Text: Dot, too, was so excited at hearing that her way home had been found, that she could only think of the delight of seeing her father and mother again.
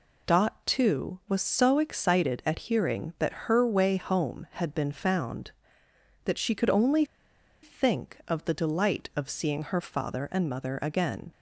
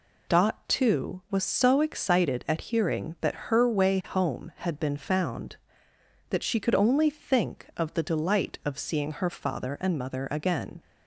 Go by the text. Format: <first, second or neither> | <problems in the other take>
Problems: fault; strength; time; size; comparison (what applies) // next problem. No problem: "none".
second | pauses between "only" and "think"; noticeable; at 7.0 s; 0.57 s long